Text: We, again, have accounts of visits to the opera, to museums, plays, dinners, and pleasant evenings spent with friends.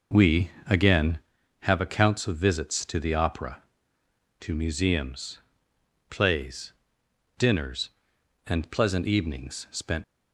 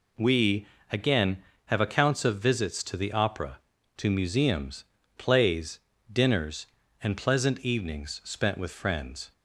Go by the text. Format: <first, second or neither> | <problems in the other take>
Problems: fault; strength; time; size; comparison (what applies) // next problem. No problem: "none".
second | stops before "with friends"; at 10.0 s